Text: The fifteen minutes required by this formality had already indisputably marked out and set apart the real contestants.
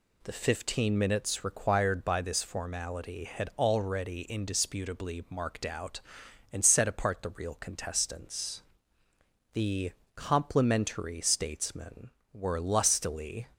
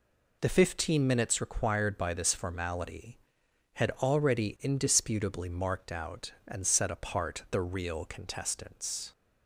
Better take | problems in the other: second | goes on to say "The complimentary statesmen were lustily"; strong; from 9.5 s on; 3.9 s long

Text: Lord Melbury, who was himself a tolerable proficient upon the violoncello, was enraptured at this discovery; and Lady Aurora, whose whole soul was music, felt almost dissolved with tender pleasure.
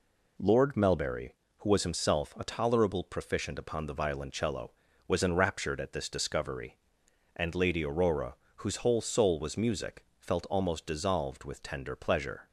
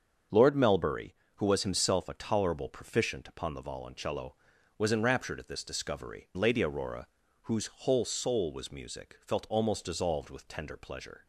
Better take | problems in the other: first | starts louder than the rest; until 1.5 s; 7 dB // skips "and"; at 6.3 s

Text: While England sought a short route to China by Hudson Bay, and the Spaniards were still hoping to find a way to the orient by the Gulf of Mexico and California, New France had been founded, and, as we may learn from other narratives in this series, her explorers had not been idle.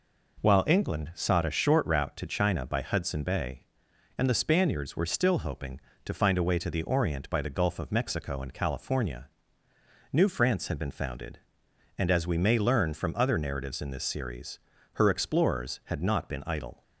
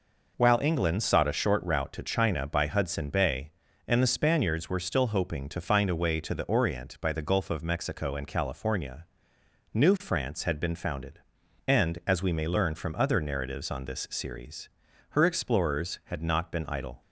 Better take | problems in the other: first | says "on" for "in"; at 13.7 s

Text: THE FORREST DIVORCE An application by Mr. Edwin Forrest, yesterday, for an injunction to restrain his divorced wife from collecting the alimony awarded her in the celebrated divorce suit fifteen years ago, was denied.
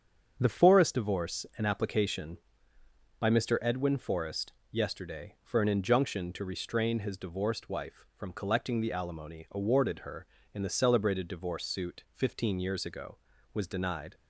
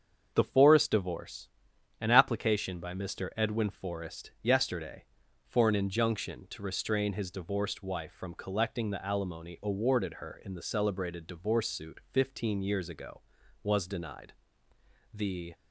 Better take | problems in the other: first | starts louder than the rest; until 1.3 s; 7 dB; strong in the first // pauses between "DIVORCE" and "An"; noticeable; at 1.4 s; 0.50 s long // goes on to say "The"; slight; from 15.1 s on; 0.42 s long

